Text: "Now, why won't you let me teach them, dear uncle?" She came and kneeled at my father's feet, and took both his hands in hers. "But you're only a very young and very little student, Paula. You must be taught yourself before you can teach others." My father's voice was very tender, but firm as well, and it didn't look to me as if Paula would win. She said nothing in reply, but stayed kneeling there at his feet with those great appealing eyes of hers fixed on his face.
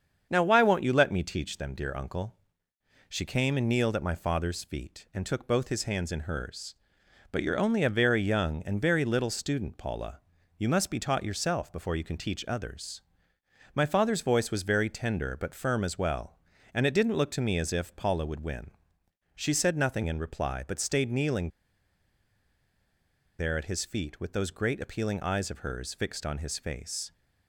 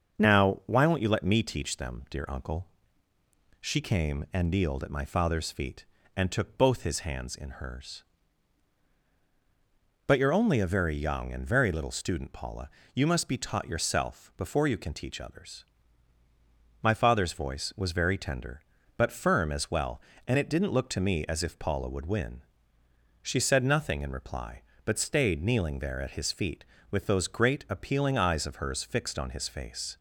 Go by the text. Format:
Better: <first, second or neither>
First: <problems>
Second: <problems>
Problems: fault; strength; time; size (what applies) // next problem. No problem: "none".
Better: second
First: starts louder than the rest; strong; until 1.3 s; 7.5 dB // pauses between "kneeling" and "there"; strong; at 21.4 s; 1.9 s long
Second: starts louder than the rest; until 1.2 s; 6.5 dB